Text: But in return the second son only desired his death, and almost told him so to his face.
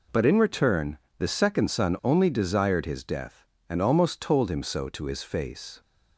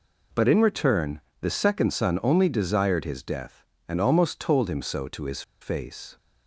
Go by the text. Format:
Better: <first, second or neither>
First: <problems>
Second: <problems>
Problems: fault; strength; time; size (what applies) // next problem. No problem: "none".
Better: first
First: pauses between "return" and "the"; slight; at 0.9 s; 0.22 s long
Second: pauses between "return" and "the"; slight; at 1.1 s; 0.22 s long // pauses between "his" and "face"; slight; at 5.4 s; 0.19 s long